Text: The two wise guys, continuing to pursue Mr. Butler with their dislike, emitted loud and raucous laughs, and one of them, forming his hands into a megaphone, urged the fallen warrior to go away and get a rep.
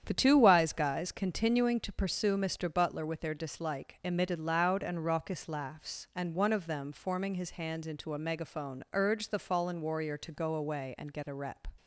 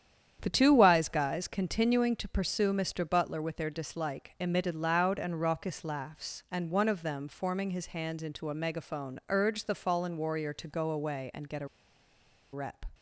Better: first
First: starts louder than the rest; strong; until 1.0 s; 9 dB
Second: starts louder than the rest; strong; until 1.4 s; 9 dB // pauses between "a" and "rep"; noticeable; at 11.6 s; 0.86 s long

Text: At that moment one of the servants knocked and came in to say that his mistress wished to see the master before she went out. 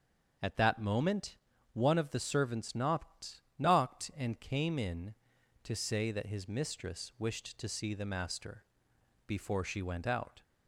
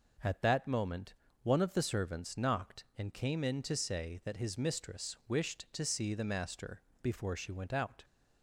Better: second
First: starts louder than the rest; until 1.7 s; 6.5 dB // pauses between "moment" and "one"; slight; at 1.3 s; 0.36 s long // says "knocked" twice; at 3.5 s // pauses between "master" and "before"; noticeable; at 8.6 s; 0.64 s long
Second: pauses between "moment" and "one"; slight; at 1.1 s; 0.30 s long // pauses between "master" and "before"; slight; at 6.8 s; 0.20 s long

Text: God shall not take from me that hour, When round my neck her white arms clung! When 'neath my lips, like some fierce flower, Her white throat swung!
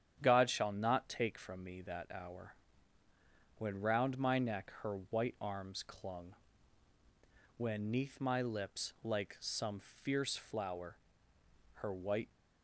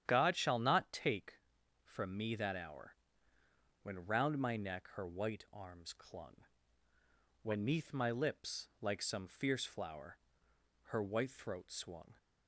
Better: second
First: starts louder than the rest; strong; until 1.2 s; 9.5 dB // stops before "throat swung"; at 12.3 s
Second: starts louder than the rest; strong; until 1.0 s; 9.5 dB

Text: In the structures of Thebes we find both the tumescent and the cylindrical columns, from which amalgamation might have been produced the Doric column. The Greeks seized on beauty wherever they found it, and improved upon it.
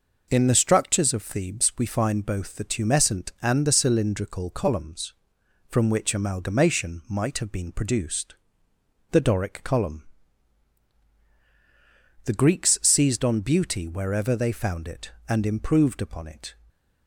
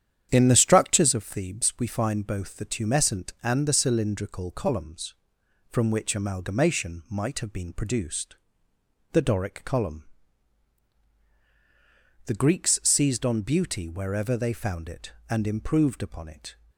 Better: first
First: pauses between "produced" and "the"; noticeable; at 8.3 s; 0.76 s long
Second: starts louder than the rest; strong; until 1.2 s; 9.5 dB // pauses between "produced" and "the"; noticeable; at 8.3 s; 0.76 s long

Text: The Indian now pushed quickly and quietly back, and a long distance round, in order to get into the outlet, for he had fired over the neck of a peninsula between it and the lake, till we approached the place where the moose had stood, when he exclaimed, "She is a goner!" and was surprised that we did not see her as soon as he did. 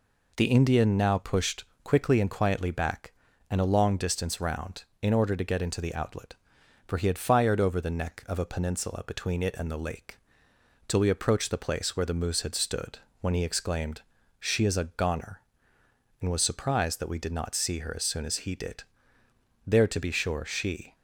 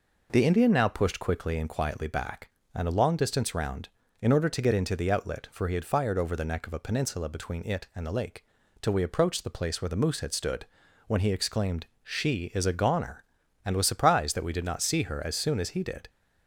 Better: second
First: pauses between "pushed" and "quickly"; slight; at 1.6 s; 0.20 s long // goes on to say "There to be sure she"; noticeable; from 19.6 s on; 1.2 s long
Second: none

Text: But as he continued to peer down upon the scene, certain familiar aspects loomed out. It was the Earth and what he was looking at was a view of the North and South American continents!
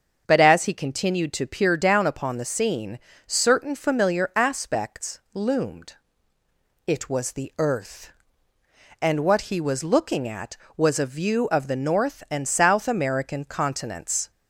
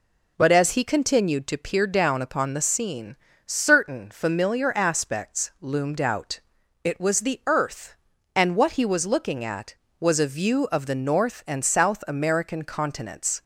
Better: second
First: starts louder than the rest; until 1.2 s; 7 dB // skips "out"; at 6.3 s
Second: none

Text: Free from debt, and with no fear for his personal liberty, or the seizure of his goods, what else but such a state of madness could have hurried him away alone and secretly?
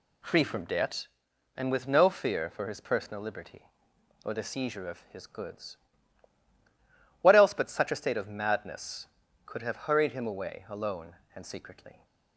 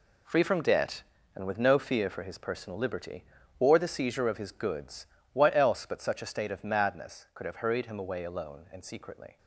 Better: neither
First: none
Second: none

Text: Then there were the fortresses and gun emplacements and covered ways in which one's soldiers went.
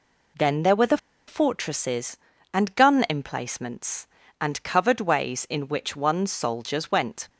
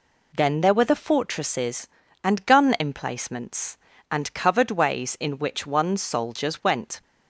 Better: second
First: pauses between "the" and "fortresses"; slight; at 0.9 s; 0.30 s long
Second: none

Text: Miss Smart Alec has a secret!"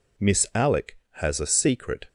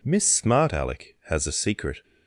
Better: second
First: skips "Smart"; at 0.5 s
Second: none

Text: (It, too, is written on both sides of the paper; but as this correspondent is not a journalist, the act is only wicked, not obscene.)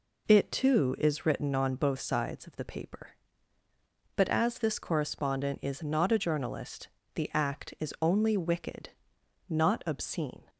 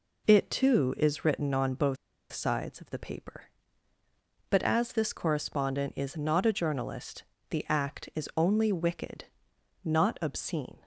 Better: first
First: none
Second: pauses between "both" and "sides"; slight; at 1.9 s; 0.35 s long

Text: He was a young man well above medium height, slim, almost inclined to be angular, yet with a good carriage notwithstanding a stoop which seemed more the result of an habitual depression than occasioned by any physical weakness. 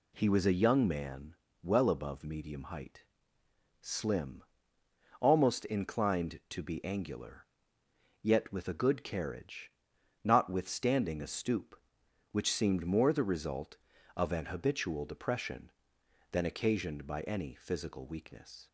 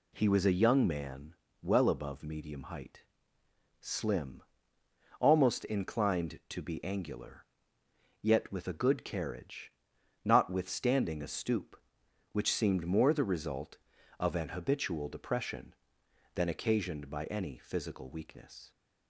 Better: neither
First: pauses between "man" and "well"; slight; at 1.3 s; 0.26 s long // pauses between "carriage" and "notwithstanding"; noticeable; at 9.7 s; 0.52 s long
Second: pauses between "man" and "well"; slight; at 1.3 s; 0.26 s long // pauses between "carriage" and "notwithstanding"; noticeable; at 9.7 s; 0.52 s long

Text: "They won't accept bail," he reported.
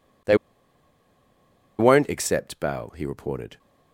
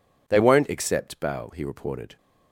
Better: second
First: pauses between "They" and "won't"; strong; at 0.3 s; 1.4 s long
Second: none

